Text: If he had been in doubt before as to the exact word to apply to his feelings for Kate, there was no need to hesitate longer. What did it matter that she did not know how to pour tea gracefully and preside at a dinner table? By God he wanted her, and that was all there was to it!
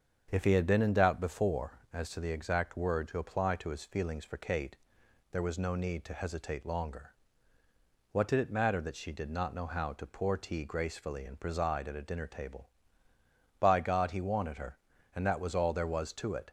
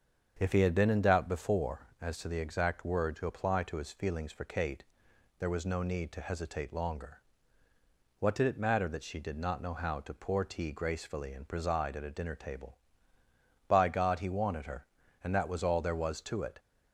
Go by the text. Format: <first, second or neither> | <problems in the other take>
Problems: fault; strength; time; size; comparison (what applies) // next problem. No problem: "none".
neither | starts louder than the rest; the same in both